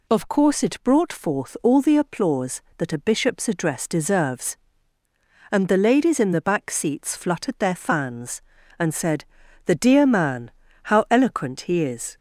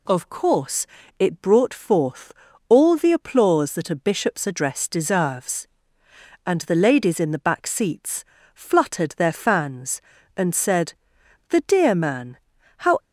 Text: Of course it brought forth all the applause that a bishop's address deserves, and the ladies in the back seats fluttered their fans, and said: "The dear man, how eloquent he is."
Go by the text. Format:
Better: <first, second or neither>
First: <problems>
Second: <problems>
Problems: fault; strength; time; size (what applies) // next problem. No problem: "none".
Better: first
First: none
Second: pauses between "course" and "it"; slight; at 0.8 s; 0.32 s long // pauses between "forth" and "all"; slight; at 2.3 s; 0.36 s long // pauses between "seats" and "fluttered"; slight; at 8.2 s; 0.32 s long // stops before "eloquent he is"; at 12.9 s